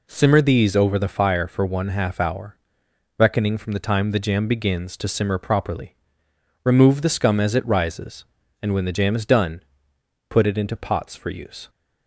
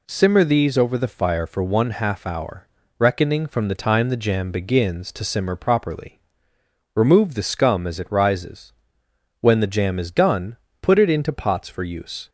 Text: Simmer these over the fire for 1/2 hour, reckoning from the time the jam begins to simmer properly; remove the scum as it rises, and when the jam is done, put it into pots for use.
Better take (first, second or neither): first